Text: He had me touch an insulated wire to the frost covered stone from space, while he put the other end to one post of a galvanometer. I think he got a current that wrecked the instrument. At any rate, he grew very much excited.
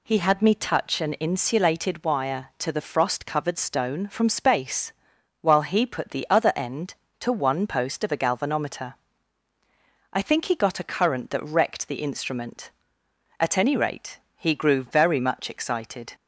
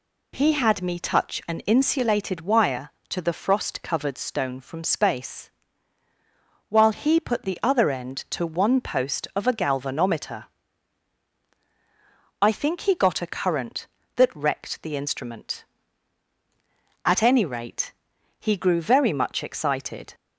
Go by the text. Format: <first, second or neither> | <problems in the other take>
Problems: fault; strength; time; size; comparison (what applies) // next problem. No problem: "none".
neither | none